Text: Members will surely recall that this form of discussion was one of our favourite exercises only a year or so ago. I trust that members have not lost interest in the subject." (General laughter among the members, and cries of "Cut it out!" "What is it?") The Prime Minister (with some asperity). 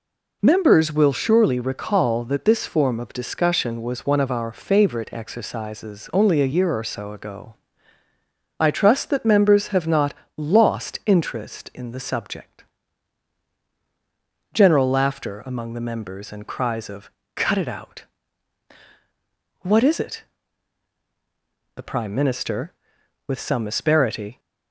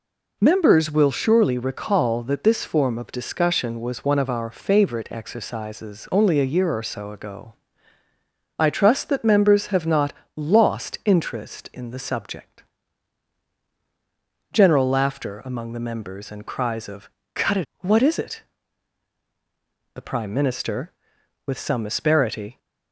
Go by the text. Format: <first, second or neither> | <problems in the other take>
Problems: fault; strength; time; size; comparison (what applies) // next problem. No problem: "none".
first | pauses between "not" and "lost"; slight; at 10.1 s; 0.22 s long; slight in the first // pauses between "of" and "Cut"; slight; at 17.0 s; 0.26 s long; slight in the first // skips "out"; at 17.7 s